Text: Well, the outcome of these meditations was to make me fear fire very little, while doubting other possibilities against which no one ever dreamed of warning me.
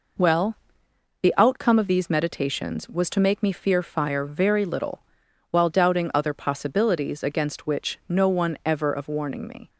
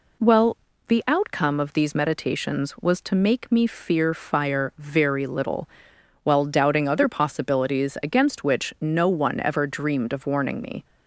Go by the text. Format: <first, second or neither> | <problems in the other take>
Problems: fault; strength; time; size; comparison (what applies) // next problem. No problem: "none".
second | skips "dreamed"; at 8.9 s